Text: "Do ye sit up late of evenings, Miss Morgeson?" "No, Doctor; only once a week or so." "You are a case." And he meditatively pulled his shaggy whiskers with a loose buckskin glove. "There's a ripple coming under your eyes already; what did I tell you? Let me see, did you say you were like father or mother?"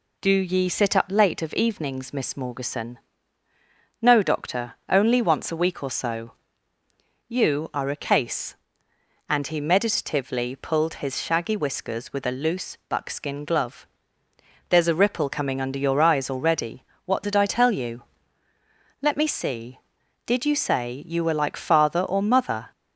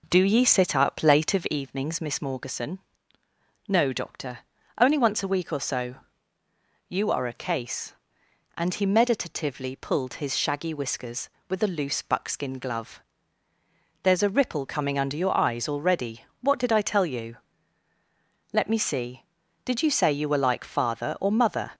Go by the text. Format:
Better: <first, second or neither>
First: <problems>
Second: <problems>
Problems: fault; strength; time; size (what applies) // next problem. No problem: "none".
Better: first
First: none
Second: starts louder than the rest; noticeable; until 1.6 s; 5 dB